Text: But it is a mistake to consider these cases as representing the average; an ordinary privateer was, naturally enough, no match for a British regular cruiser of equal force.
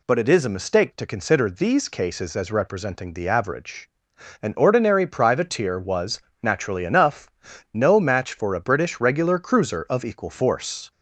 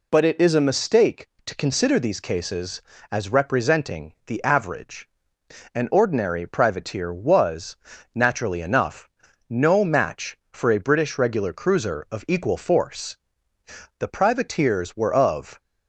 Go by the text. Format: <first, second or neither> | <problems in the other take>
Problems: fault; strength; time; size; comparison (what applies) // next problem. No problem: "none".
first | goes on to say "The privateers were of"; from 13.9 s on; 1.6 s long